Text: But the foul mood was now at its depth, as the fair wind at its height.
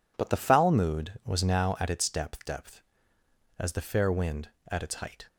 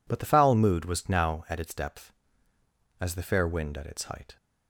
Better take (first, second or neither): second